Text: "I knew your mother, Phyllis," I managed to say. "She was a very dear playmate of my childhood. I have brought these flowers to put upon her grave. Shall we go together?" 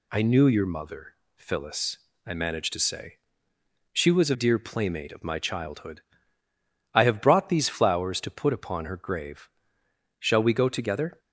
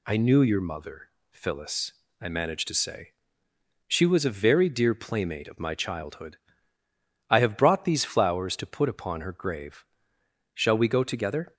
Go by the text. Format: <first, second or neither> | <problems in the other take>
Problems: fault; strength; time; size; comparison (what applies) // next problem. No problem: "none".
second | skips "very"; at 4.3 s